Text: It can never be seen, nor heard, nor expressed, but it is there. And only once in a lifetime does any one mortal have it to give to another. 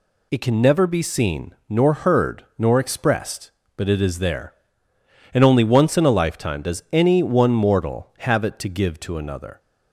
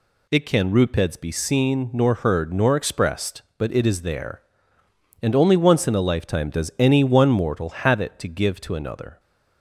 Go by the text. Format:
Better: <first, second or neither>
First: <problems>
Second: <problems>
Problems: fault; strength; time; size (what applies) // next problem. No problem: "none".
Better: first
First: none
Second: says "rupeds" for "never"; at 0.7 s